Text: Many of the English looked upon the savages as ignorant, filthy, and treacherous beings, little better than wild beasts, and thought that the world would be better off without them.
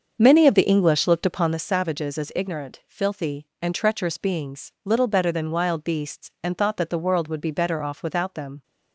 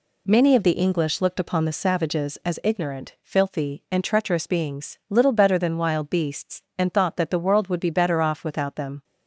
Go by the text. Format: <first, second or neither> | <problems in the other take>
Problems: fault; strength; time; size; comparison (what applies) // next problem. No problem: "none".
second | starts louder than the rest; until 1.7 s; 6.5 dB